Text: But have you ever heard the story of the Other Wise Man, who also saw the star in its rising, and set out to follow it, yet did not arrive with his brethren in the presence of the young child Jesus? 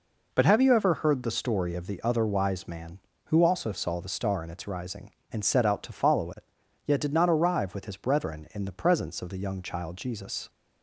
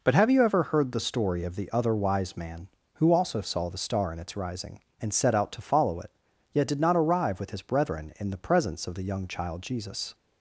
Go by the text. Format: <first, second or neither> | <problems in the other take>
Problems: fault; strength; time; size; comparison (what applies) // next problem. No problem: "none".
neither | none